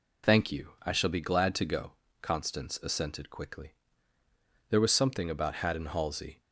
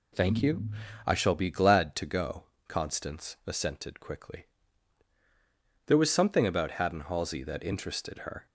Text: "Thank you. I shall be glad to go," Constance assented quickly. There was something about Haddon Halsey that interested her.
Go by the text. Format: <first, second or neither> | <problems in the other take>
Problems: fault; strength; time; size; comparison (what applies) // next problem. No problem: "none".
second | stops before "that interested her"; at 6.4 s